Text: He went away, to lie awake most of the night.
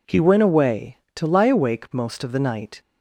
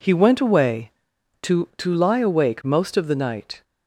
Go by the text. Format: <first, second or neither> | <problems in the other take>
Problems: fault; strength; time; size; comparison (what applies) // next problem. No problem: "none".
first | says "to" twice; at 1.7 s